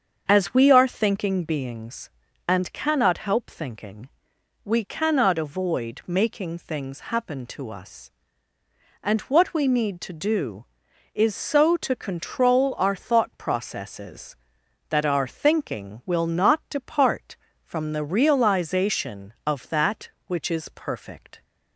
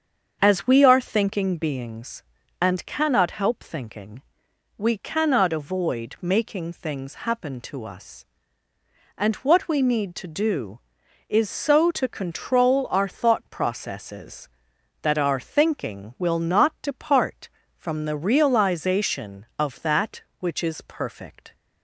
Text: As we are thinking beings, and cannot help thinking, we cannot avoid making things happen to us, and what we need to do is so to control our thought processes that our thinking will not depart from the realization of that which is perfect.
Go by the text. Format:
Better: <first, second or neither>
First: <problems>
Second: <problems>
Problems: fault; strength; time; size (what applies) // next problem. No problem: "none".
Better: neither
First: starts louder than the rest; strong; until 1.2 s; 7 dB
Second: starts louder than the rest; strong; until 1.4 s; 7 dB